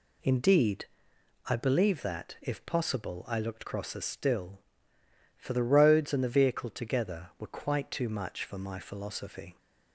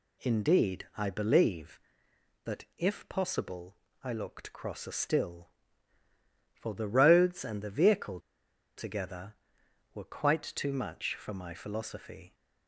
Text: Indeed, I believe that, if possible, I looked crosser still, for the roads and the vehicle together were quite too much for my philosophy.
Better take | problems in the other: first | pauses between "vehicle" and "together"; noticeable; at 8.1 s; 0.58 s long

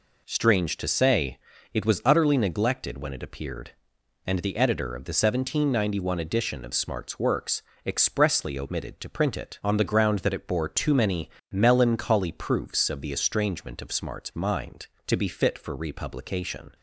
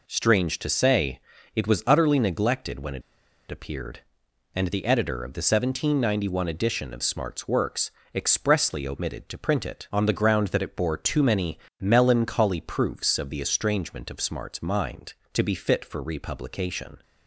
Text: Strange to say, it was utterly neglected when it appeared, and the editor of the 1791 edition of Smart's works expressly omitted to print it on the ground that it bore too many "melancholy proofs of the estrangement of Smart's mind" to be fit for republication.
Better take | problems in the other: first | pauses between "it" and "appeared"; noticeable; at 3.0 s; 0.48 s long // pauses between "works" and "expressly"; slight; at 7.9 s; 0.20 s long; slight in the first // pauses between "many" and "melancholy"; slight; at 11.5 s; 0.22 s long; slight in the first

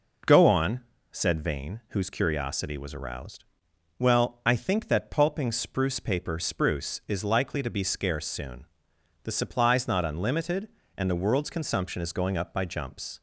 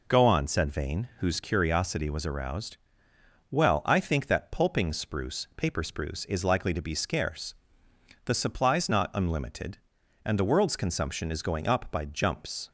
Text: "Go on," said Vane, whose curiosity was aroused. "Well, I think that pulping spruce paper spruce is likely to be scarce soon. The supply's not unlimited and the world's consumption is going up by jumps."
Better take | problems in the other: first | skips "soon"; at 7.8 s

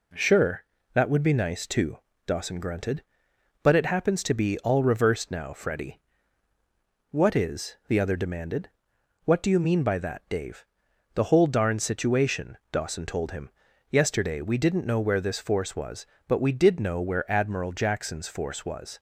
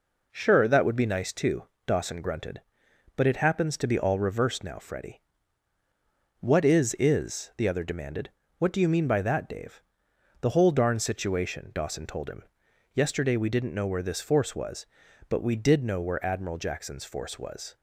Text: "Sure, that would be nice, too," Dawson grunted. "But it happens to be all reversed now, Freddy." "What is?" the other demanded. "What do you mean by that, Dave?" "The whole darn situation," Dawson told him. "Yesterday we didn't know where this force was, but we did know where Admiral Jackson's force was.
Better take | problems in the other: first | says "is" twice; at 6.9 s

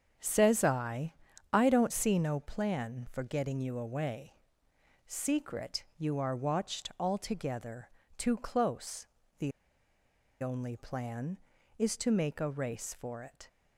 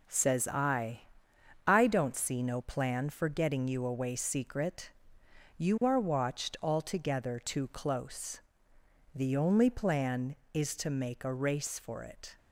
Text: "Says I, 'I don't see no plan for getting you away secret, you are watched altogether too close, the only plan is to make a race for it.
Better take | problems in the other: second | starts louder than the rest; strong; until 1.5 s; 8 dB // pauses between "away" and "secret"; noticeable; at 4.3 s; 0.72 s long // pauses between "altogether" and "too"; slight; at 7.8 s; 0.28 s long // pauses between "the" and "only"; noticeable; at 9.5 s; 0.92 s long

